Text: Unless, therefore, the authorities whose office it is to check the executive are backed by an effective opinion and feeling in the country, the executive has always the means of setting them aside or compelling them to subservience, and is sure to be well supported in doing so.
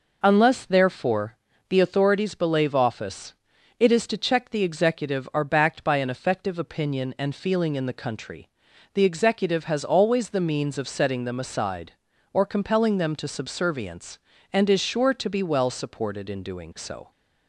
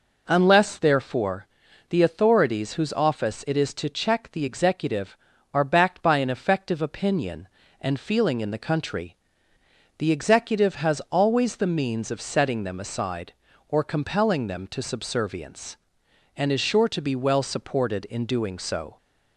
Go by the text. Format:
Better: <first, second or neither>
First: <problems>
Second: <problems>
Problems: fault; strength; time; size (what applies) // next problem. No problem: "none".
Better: second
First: says "belave" for "whose"; at 2.3 s // pauses between "office" and "it"; noticeable; at 3.3 s; 0.46 s long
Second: none